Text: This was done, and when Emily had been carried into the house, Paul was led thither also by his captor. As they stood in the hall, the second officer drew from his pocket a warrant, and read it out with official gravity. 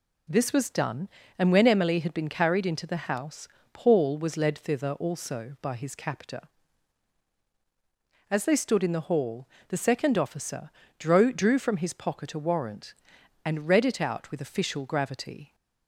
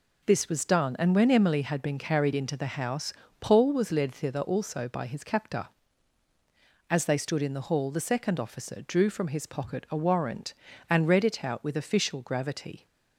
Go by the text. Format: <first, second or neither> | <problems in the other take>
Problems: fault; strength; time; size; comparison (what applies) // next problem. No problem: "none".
second | pauses between "officer" and "drew"; slight; at 10.6 s; 0.28 s long // says "drew" twice; at 11.3 s